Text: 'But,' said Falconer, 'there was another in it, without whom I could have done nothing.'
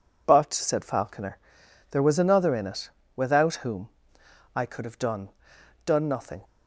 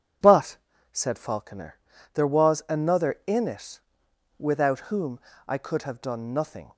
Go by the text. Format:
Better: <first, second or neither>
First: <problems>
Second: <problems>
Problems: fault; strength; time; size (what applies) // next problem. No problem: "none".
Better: second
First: pauses between "whom" and "I"; noticeable; at 3.8 s; 0.66 s long // says "done" twice; at 5.8 s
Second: pauses between "whom" and "I"; slight; at 5.1 s; 0.28 s long